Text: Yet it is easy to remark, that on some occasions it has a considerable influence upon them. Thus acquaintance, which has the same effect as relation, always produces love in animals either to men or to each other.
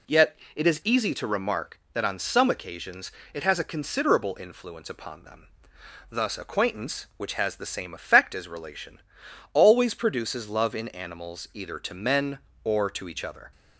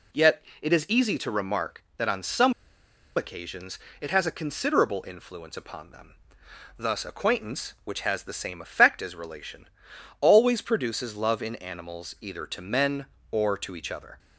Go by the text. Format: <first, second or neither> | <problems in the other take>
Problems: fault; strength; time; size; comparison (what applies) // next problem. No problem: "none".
first | pauses between "Yet" and "it"; slight; at 0.4 s; 0.18 s long; slight in the first // pauses between "some" and "occasions"; noticeable; at 2.5 s; 0.63 s long // pauses between "occasions" and "it"; slight; at 3.7 s; 0.22 s long; slight in the first